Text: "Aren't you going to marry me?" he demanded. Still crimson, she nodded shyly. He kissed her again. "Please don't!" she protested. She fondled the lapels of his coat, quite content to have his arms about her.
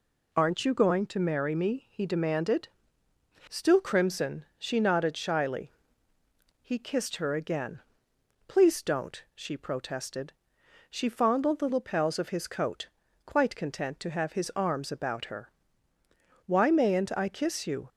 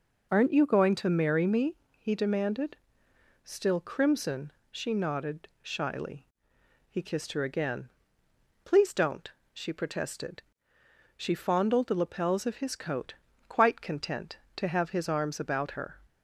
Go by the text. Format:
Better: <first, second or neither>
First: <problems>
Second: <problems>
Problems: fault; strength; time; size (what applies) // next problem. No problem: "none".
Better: second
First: goes on to say "Why mayn't I kiss you"; from 16.4 s on; 1.4 s long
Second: none